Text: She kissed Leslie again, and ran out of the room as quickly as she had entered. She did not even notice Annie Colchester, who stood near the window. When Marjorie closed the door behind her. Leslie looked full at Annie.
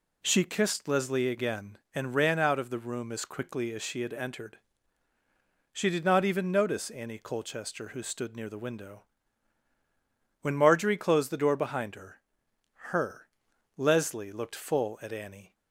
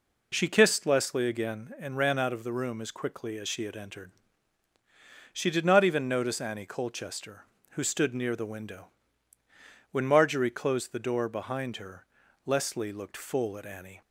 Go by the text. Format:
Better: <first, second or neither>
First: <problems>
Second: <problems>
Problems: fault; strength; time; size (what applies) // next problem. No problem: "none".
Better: second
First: says "her" twice; at 12.9 s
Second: none